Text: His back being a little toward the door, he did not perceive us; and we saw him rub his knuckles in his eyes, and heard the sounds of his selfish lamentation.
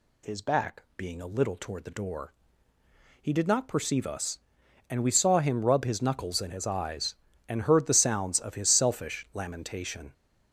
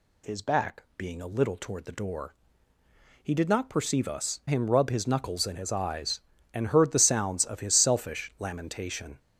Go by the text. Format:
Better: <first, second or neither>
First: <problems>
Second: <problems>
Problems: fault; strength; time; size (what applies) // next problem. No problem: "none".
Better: first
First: none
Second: skips "and we saw"; at 4.4 s